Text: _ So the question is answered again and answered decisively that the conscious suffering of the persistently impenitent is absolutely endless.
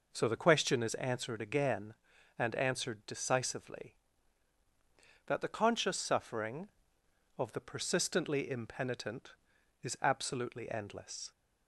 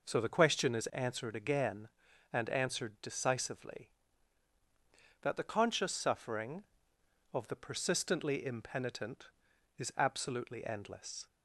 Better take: neither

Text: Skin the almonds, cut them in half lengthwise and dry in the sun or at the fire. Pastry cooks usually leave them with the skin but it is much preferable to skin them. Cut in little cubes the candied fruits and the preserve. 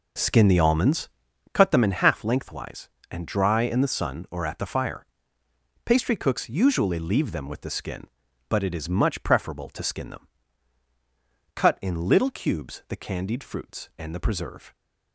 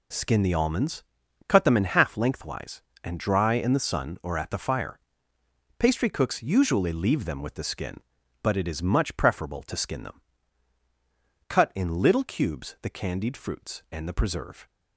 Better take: second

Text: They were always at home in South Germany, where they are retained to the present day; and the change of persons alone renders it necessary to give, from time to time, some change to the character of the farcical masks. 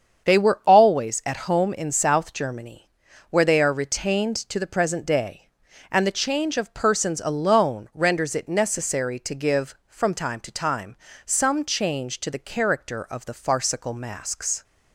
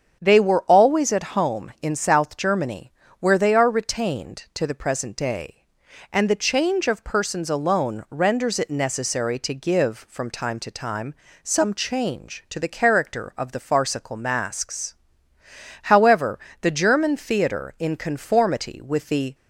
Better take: first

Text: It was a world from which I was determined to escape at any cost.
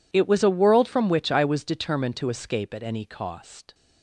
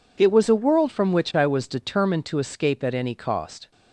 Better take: neither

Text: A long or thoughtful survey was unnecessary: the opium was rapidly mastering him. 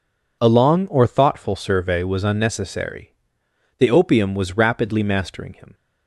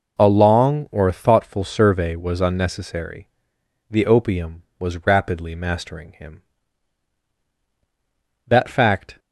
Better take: first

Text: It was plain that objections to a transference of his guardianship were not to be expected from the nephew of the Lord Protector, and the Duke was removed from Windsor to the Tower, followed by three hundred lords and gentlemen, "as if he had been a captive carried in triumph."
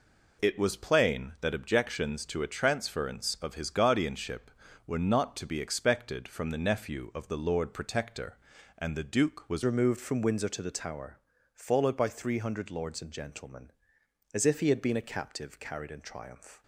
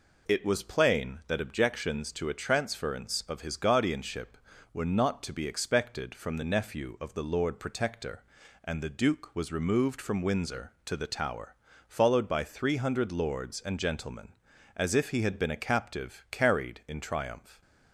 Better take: second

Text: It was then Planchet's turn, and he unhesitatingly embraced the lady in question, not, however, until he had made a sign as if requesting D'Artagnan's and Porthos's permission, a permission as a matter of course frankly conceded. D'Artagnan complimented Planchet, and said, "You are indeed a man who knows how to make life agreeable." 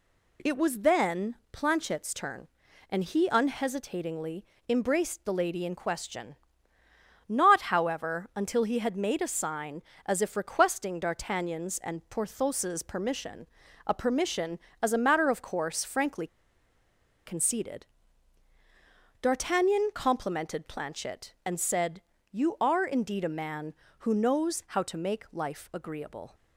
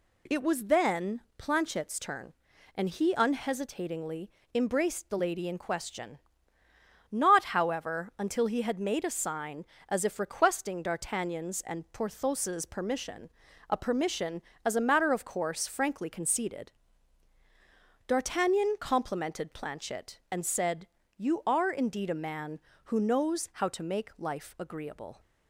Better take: second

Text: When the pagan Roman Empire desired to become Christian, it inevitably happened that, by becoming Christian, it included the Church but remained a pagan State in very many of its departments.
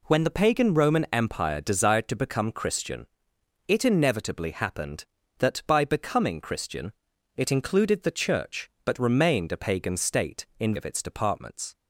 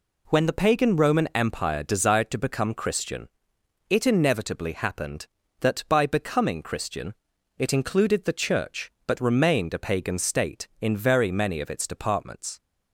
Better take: second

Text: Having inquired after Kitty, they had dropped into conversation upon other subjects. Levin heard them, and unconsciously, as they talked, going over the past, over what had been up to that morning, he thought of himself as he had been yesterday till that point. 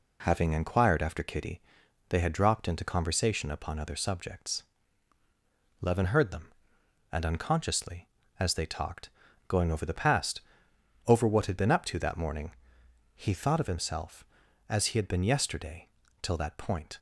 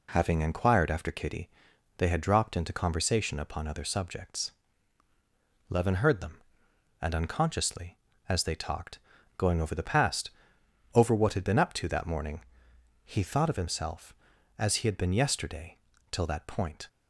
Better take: neither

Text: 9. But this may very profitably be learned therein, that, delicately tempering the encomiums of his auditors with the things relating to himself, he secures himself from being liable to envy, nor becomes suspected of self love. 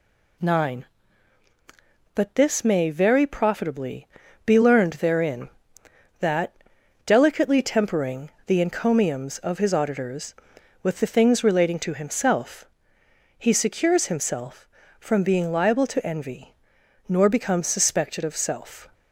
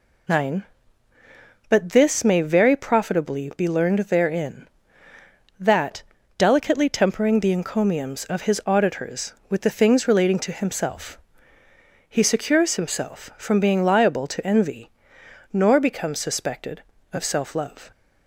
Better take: second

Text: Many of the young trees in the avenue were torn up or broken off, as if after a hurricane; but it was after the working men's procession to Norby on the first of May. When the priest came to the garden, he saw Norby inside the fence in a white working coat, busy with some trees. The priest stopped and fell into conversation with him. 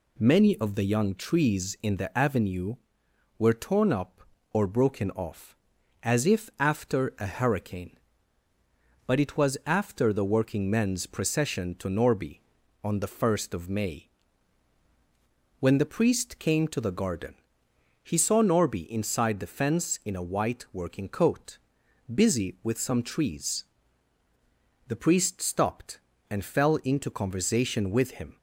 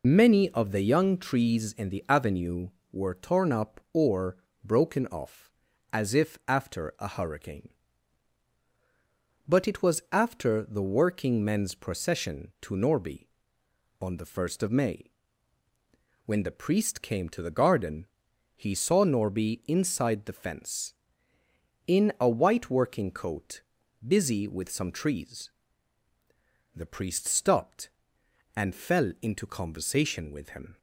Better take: first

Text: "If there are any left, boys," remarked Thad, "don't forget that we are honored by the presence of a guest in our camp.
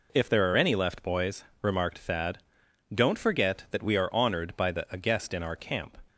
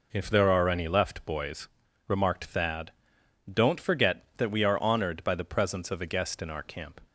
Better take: second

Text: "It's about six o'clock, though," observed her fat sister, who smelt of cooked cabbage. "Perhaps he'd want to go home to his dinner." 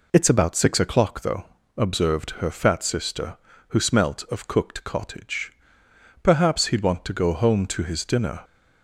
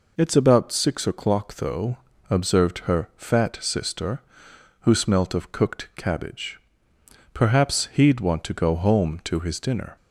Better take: second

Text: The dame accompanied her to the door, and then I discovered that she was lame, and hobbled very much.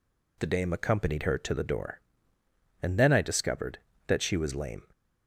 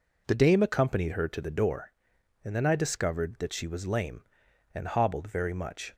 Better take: second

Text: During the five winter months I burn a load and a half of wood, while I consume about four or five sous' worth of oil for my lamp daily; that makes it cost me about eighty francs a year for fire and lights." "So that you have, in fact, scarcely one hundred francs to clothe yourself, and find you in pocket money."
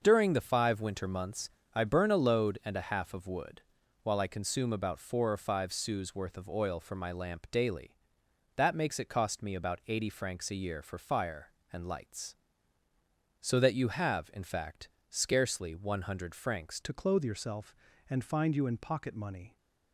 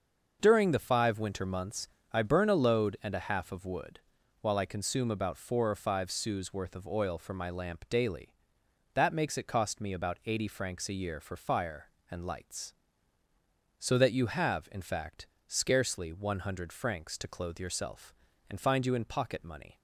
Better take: second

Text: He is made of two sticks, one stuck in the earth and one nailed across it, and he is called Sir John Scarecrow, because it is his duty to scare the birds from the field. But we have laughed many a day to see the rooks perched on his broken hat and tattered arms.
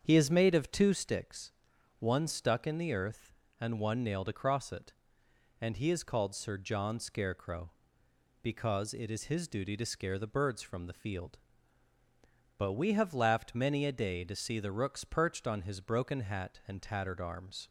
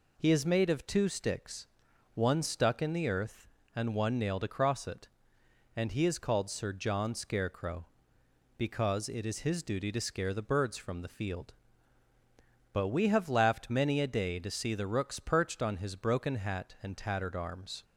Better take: second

